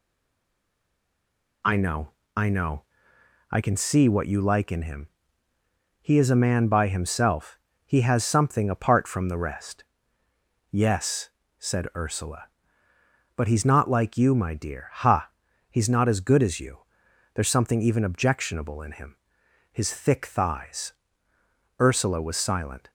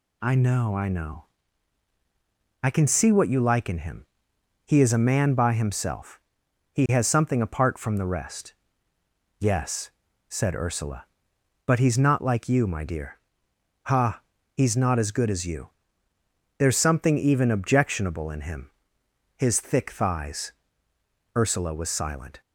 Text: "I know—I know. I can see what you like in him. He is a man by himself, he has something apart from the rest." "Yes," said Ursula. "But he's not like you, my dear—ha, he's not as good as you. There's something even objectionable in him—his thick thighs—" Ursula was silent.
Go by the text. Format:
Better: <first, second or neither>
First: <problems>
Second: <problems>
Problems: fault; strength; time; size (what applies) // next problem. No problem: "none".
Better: second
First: stays silent before the first word; noticeable; until 1.6 s; 1.6 s long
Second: none